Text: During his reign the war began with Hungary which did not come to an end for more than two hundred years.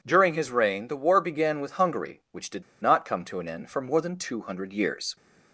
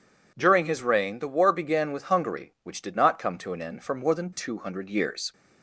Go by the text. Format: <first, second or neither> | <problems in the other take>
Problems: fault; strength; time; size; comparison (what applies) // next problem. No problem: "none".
second | pauses between "did" and "not"; slight; at 2.6 s; 0.18 s long